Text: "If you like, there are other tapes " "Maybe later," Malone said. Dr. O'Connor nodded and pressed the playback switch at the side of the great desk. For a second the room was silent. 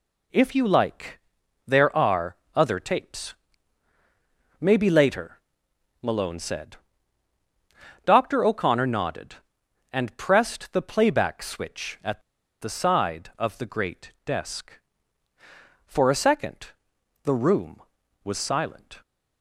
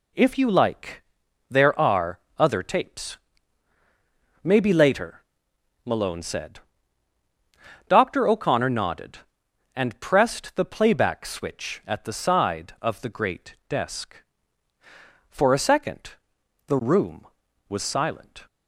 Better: second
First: pauses between "are" and "other"; slight; at 2.3 s; 0.20 s long // pauses between "at" and "the"; at 12.2 s; 0.40 s long // pauses between "second" and "the"; noticeable; at 16.6 s; 0.52 s long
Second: pauses between "are" and "other"; slight; at 2.1 s; 0.20 s long // pauses between "second" and "the"; noticeable; at 16.1 s; 0.52 s long

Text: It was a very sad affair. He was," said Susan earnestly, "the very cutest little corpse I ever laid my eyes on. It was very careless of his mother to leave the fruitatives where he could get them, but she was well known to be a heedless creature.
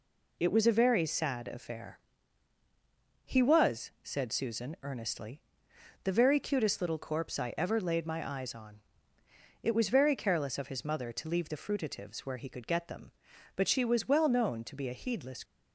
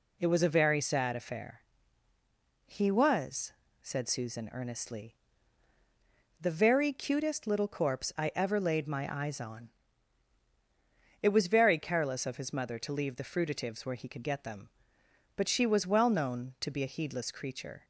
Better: second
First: stops before "creature"; at 15.4 s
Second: none

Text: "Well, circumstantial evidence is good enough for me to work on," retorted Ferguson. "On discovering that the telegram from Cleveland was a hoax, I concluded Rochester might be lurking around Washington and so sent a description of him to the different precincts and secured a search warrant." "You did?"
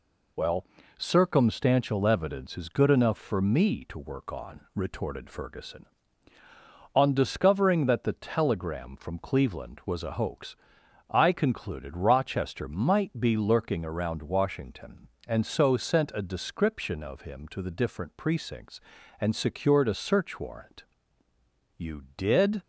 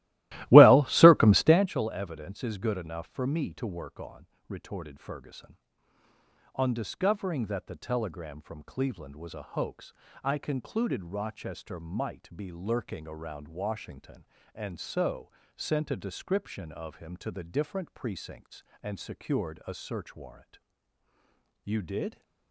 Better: first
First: none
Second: starts louder than the rest; strong; until 1.7 s; 17 dB // pauses between "so" and "sent"; slight; at 15.3 s; 0.24 s long

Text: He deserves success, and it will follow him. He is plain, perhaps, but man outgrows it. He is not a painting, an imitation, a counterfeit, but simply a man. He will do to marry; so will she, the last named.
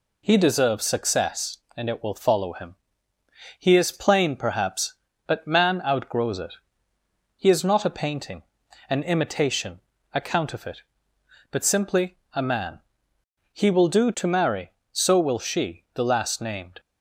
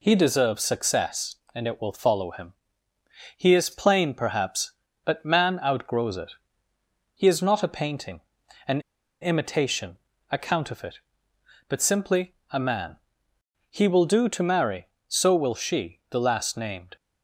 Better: first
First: pauses between "simply" and "a"; slight; at 12.1 s; 0.16 s long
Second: pauses between "an" and "imitation"; at 8.8 s; 0.41 s long // pauses between "simply" and "a"; slight; at 12.3 s; 0.16 s long

